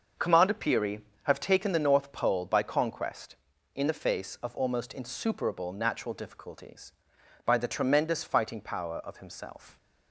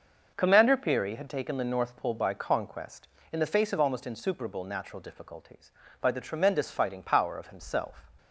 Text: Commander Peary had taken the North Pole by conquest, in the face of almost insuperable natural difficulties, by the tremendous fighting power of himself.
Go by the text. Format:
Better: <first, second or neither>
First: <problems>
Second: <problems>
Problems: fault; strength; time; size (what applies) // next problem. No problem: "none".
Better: second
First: starts louder than the rest; until 1.3 s; 6.5 dB // says "have" for "had"; at 1.2 s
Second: starts louder than the rest; until 1.3 s; 6.5 dB